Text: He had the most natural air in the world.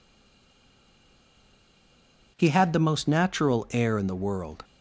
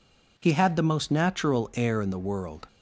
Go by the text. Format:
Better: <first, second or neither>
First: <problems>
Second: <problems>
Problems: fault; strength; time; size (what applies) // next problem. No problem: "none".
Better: second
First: stays silent before the first word; until 2.3 s; 2.3 s long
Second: none